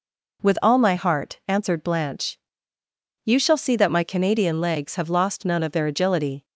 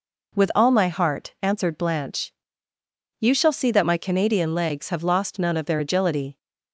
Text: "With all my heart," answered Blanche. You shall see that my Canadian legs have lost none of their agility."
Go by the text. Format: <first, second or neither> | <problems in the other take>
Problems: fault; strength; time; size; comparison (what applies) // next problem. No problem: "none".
neither | none